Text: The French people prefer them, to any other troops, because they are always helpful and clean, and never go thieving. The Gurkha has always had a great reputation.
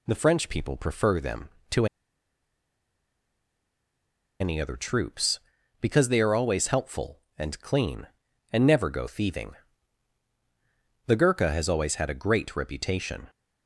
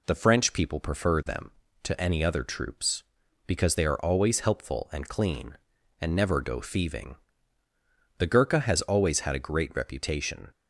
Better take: second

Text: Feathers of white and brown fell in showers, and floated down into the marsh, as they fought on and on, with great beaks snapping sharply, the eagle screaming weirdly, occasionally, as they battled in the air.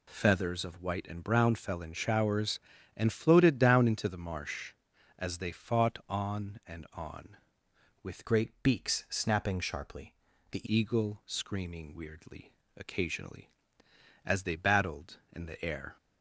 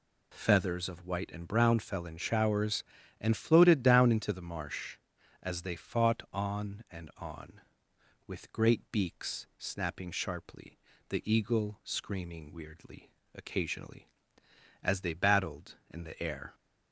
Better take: second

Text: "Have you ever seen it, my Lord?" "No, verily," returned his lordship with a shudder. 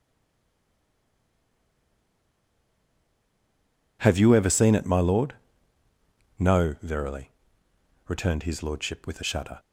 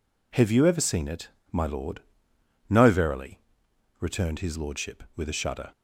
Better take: second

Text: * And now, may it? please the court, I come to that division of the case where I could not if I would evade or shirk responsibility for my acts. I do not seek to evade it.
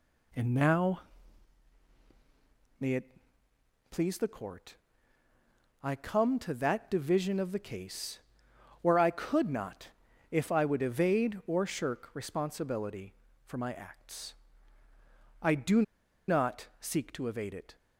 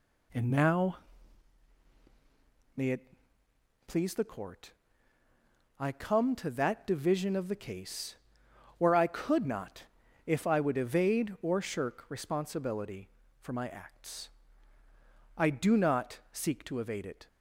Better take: second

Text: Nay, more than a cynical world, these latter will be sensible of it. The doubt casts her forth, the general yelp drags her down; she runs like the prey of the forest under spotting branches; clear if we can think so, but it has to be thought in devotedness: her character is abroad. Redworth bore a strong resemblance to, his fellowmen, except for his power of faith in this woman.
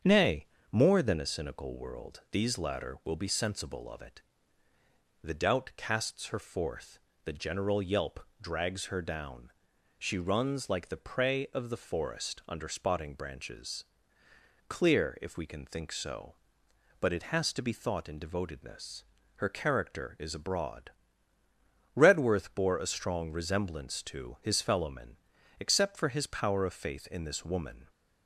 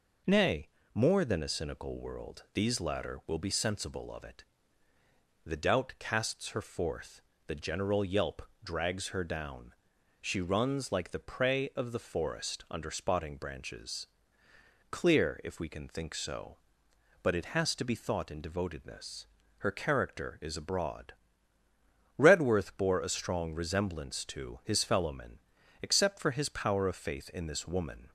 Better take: second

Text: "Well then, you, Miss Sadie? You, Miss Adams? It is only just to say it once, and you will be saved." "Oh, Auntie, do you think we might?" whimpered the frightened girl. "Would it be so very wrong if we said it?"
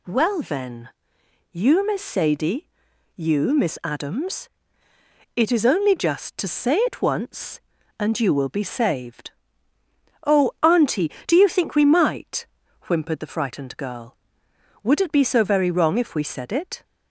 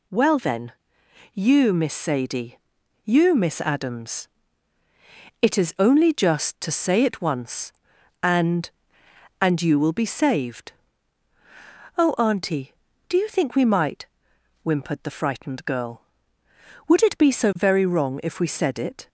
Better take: first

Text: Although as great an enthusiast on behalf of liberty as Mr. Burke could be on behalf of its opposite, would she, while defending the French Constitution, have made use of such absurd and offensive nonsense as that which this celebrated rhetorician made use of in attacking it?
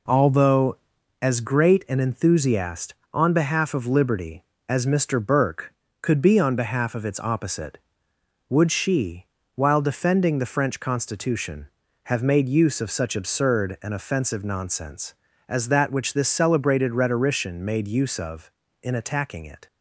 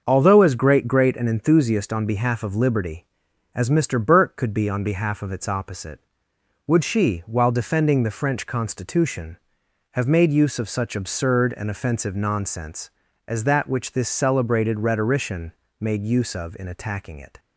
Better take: first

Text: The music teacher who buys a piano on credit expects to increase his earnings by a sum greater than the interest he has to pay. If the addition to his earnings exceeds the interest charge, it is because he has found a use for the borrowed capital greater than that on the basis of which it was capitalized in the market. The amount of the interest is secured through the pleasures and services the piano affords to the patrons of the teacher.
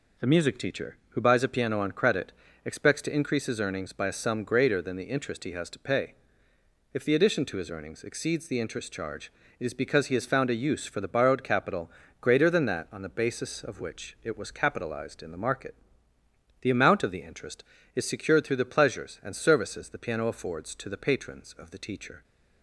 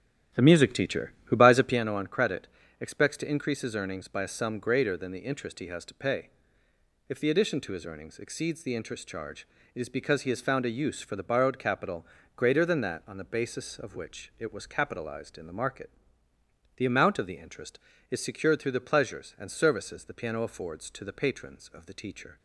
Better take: first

